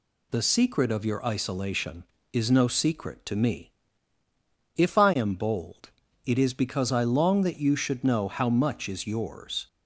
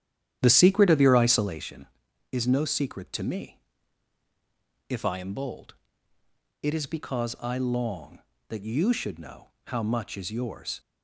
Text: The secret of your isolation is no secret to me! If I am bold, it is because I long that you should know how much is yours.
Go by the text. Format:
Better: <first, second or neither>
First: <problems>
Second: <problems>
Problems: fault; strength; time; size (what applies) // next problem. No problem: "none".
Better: first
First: none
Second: starts louder than the rest; strong; until 1.6 s; 11 dB // pauses between "know" and "how"; slight; at 9.4 s; 0.16 s long